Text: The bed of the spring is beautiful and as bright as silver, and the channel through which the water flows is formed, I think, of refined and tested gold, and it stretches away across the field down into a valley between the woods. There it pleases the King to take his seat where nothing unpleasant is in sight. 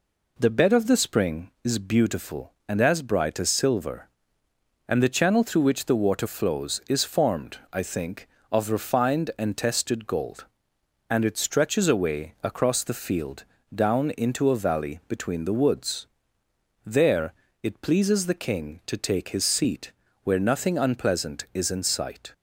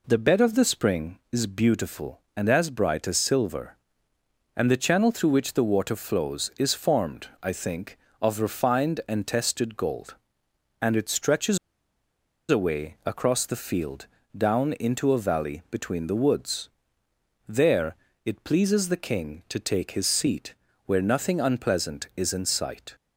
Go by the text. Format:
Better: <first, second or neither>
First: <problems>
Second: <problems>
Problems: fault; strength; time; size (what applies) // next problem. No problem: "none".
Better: first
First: pauses between "field" and "down"; slight; at 13.4 s; 0.30 s long // pauses between "There" and "it"; slight; at 17.3 s; 0.26 s long // pauses between "seat" and "where"; slight; at 19.9 s; 0.30 s long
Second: pauses between "stretches" and "away"; noticeable; at 11.5 s; 0.91 s long // pauses between "field" and "down"; slight; at 14.0 s; 0.30 s long // pauses between "There" and "it"; slight; at 17.9 s; 0.26 s long // pauses between "seat" and "where"; slight; at 20.5 s; 0.30 s long